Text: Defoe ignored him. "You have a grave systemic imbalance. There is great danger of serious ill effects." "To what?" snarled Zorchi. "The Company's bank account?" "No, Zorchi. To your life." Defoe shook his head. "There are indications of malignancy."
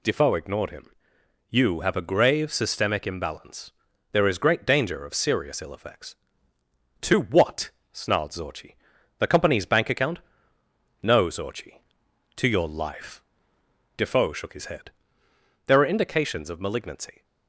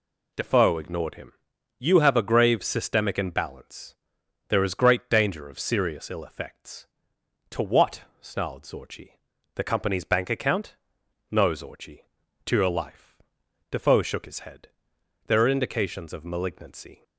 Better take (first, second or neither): neither